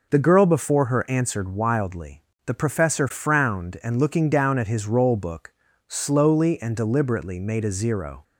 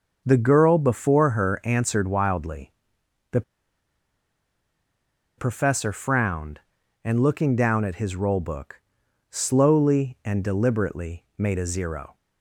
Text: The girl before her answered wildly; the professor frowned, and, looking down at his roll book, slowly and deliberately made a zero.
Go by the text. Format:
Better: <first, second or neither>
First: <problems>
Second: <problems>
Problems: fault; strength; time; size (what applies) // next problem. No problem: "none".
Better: first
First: none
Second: starts louder than the rest; until 1.2 s; 6 dB // pauses between "the" and "professor"; strong; at 3.4 s; 1.9 s long